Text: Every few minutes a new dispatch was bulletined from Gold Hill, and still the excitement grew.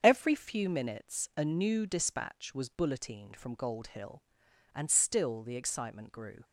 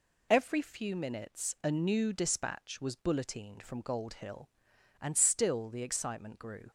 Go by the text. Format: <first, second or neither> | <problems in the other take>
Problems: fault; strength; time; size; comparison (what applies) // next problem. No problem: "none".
second | starts louder than the rest; strong; until 1.0 s; 7 dB